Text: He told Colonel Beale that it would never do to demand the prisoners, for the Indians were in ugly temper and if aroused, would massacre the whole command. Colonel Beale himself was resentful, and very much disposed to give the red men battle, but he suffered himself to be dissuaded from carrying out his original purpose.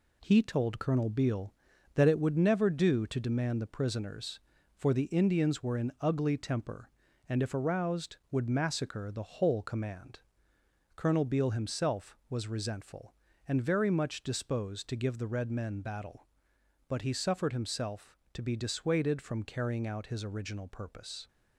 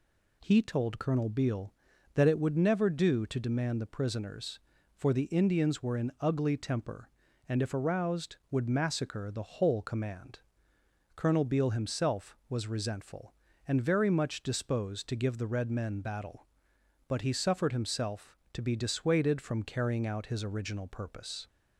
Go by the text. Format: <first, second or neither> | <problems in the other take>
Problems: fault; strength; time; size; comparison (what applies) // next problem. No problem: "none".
second | gets quieter; noticeable; throughout; 5.5 dB